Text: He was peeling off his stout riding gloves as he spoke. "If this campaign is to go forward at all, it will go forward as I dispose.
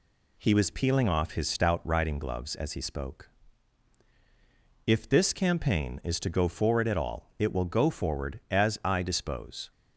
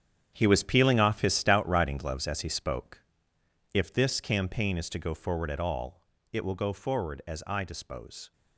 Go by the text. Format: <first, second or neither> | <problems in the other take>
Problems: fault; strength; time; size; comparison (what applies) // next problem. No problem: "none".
first | gets quieter; strong; throughout; 12.5 dB